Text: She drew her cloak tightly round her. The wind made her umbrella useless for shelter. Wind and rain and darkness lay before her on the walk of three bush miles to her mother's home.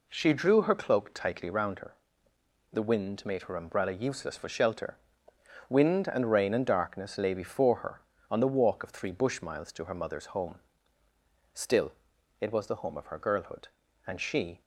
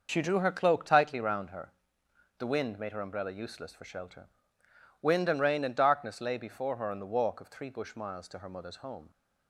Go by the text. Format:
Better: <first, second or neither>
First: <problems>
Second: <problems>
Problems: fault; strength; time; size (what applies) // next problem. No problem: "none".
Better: second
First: goes on to say "Still it was the home of her girlhood and she"; strong; from 11.5 s on; 3.0 s long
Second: none